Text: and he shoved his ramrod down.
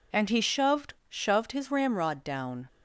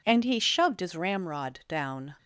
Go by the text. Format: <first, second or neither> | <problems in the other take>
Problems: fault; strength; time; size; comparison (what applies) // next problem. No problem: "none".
second | says "shoved" twice; at 1.0 s